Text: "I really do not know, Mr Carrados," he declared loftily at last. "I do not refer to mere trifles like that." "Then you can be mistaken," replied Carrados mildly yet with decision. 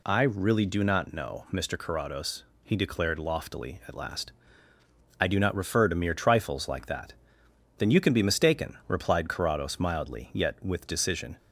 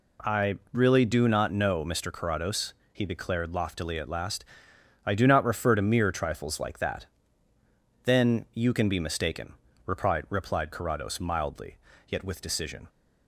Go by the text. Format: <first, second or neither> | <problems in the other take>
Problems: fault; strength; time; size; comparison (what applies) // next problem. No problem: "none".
first | says "replied" twice; at 10.2 s // pauses between "mildly" and "yet"; slight; at 11.7 s; 0.30 s long